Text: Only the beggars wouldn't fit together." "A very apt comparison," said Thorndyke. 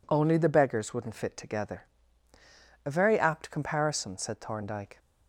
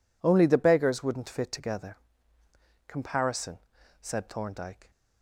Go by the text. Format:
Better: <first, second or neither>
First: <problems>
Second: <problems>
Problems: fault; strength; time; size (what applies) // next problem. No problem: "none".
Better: first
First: none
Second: skips "A very apt"; at 2.4 s